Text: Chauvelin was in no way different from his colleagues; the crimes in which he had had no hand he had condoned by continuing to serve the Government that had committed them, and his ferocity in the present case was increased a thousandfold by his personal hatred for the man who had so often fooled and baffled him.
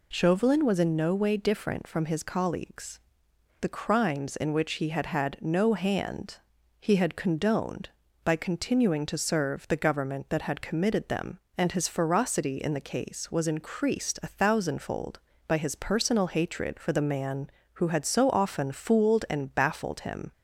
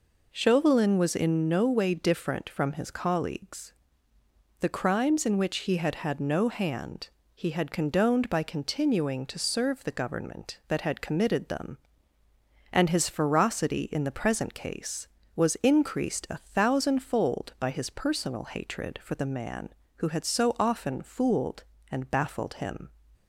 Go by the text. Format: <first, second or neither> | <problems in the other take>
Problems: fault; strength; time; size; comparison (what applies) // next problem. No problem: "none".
second | pauses between "hand" and "he"; noticeable; at 6.3 s; 0.46 s long; slight in the second // skips "present"; at 12.8 s